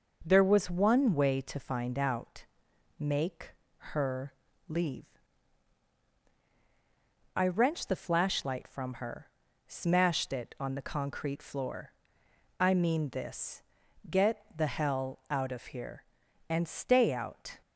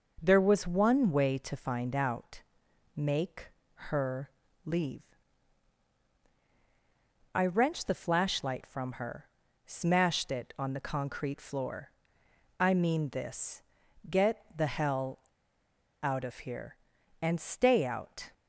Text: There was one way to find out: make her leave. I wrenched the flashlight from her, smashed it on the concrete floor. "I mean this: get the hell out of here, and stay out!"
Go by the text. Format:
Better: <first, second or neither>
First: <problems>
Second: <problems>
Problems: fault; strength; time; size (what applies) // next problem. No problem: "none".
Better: first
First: pauses between "make" and "her"; at 3.5 s; 0.42 s long // pauses between "her" and "leave"; slight; at 4.3 s; 0.36 s long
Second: pauses between "make" and "her"; at 3.4 s; 0.42 s long // pauses between "her" and "leave"; slight; at 4.2 s; 0.36 s long // pauses between "hell" and "out"; noticeable; at 15.1 s; 0.83 s long